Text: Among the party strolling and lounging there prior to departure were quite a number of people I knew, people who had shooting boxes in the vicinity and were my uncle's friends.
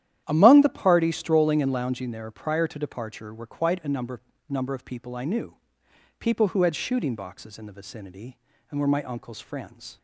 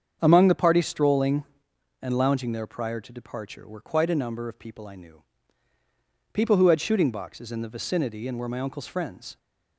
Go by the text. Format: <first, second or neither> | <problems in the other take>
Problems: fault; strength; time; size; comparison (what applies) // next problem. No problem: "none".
second | starts louder than the rest; strong; until 1.2 s; 11 dB; strong in the second // says "number" twice; at 4.4 s